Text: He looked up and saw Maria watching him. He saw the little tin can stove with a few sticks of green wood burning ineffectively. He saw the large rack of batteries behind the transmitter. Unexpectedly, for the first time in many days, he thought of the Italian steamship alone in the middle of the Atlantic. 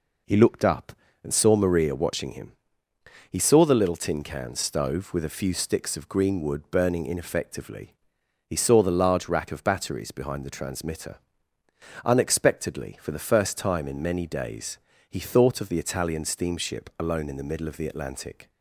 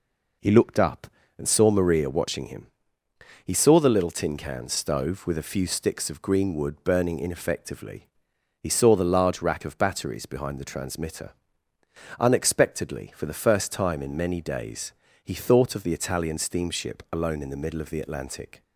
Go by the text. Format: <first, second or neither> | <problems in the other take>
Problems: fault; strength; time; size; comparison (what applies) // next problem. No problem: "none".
neither | none